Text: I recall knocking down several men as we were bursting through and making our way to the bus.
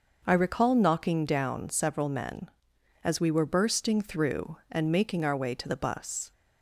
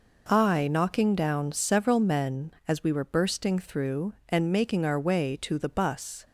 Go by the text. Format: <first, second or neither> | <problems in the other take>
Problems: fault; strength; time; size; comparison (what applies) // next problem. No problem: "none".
first | skips "recall"; at 0.6 s